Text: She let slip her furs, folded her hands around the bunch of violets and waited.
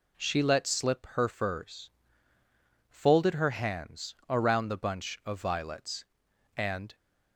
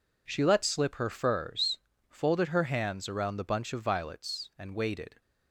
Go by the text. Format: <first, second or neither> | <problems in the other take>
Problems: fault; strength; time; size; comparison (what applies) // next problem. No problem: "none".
second | stops before "waited"; at 6.9 s